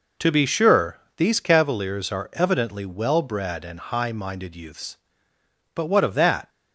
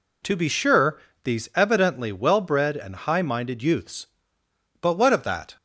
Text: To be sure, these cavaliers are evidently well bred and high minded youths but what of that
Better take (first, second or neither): first